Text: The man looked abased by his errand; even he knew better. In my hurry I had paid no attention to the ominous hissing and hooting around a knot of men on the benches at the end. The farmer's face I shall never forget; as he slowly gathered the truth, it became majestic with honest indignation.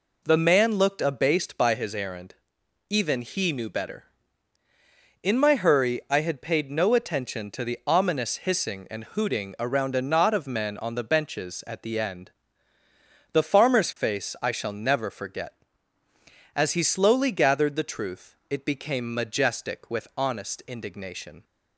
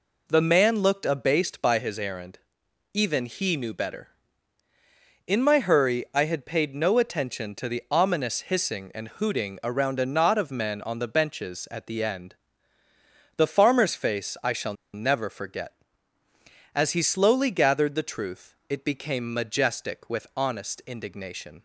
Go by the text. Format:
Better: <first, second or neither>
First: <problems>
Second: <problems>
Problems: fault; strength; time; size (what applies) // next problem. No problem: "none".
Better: first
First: none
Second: pauses between "shall" and "never"; slight; at 14.7 s; 0.20 s long